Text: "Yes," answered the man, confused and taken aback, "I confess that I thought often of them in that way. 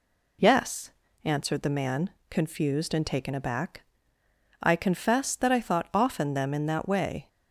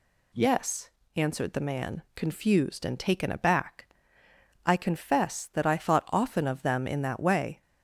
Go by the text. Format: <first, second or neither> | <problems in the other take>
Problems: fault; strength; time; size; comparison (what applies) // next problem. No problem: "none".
second | skips "of"; at 6.3 s